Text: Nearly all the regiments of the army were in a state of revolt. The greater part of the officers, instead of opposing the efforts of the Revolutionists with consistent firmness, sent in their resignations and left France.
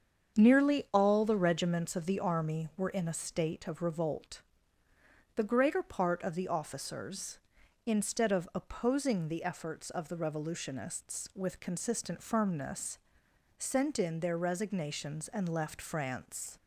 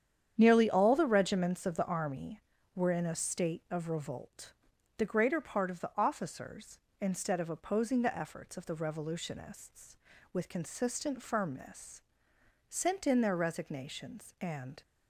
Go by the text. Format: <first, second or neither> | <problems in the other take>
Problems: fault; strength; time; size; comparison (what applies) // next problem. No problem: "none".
first | starts louder than the rest; strong; until 1.3 s; 9 dB; strong in the first // stops before "left France"; at 14.8 s